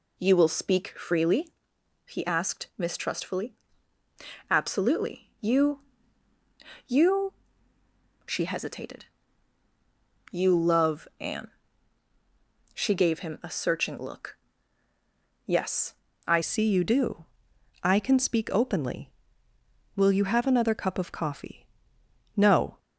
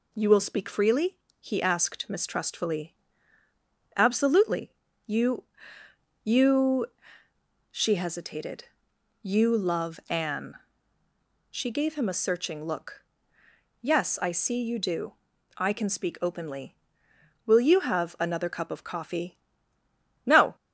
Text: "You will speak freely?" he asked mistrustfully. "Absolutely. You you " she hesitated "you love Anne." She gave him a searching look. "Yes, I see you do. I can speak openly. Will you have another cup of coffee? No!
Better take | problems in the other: second | pauses between "You" and "you"; at 5.8 s; 1.0 s long; noticeable in the second // pauses between "hesitated" and "you"; at 9.0 s; 1.2 s long; noticeable in the second // changes voice at "see"; from 16.4 s on; 6.3 s long

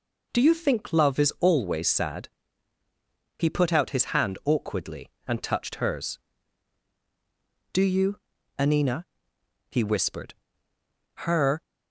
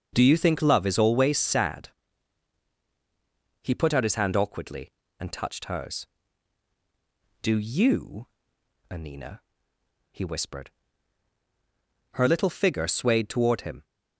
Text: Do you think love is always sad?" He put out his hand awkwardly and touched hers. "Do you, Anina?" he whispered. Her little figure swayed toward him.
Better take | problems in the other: second | stops before "little figure swayed toward him"; at 11.6 s

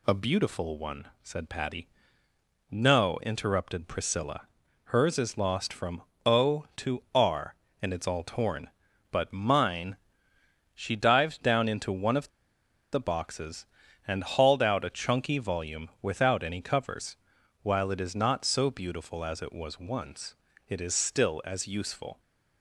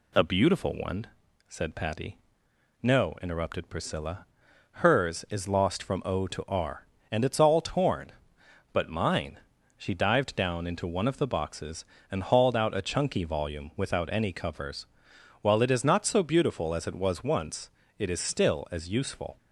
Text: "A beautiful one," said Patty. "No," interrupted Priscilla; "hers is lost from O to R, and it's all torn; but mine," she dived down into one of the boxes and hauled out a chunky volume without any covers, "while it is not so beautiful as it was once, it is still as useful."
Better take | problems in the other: second | pauses between "from" and "O"; slight; at 6.0 s; 0.24 s long // pauses between "of" and "the"; noticeable; at 12.2 s; 0.63 s long

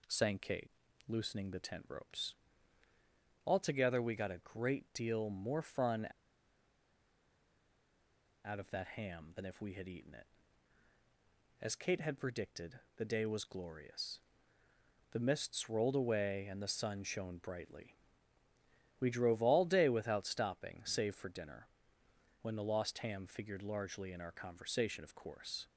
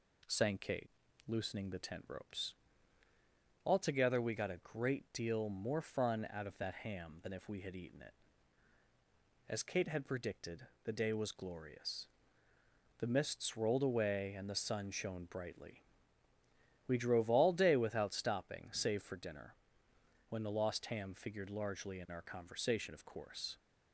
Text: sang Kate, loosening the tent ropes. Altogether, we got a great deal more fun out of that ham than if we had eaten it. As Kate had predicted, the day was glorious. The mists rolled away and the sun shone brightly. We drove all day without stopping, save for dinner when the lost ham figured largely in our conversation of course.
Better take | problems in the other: second | pauses between "fun" and "out"; strong; at 6.0 s; 2.3 s long // pauses between "dinner" and "when"; noticeable; at 21.6 s; 0.76 s long; noticeable in the second

